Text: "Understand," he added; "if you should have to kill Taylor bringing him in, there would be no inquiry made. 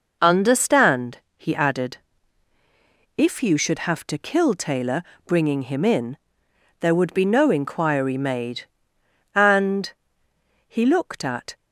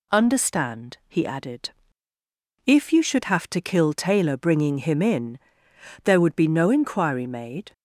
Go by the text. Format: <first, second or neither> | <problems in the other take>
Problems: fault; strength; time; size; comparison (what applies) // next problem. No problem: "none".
second | pauses between "Taylor" and "bringing"; slight; at 5.0 s; 0.24 s long // goes on to say "And he looked at"; strong; from 9.3 s on; 2.2 s long